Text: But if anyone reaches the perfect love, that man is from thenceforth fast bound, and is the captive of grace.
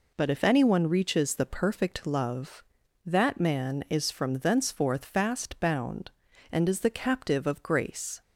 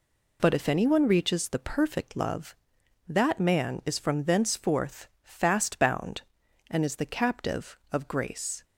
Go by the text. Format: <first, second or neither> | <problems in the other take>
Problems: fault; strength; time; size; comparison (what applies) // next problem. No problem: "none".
neither | none